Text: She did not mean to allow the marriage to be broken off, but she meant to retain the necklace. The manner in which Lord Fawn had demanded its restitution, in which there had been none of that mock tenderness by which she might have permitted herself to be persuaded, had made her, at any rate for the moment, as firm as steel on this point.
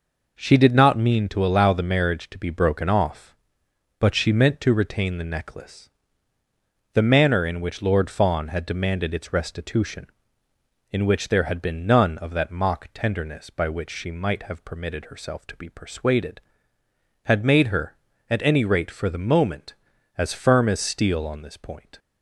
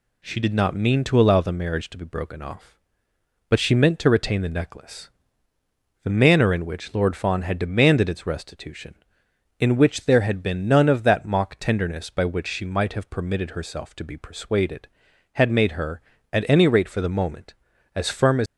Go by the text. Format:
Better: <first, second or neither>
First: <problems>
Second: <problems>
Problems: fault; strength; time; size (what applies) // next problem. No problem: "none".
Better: first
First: none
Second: stops before "steel on this point"; at 18.4 s